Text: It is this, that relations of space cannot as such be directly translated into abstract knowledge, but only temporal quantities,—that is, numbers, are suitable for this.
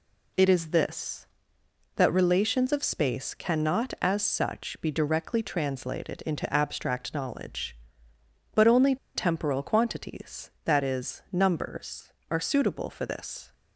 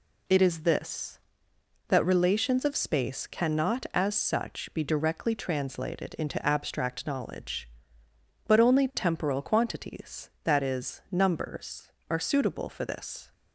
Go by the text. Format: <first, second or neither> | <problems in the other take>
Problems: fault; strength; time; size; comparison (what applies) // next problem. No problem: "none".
second | pauses between "only" and "temporal"; slight; at 8.9 s; 0.19 s long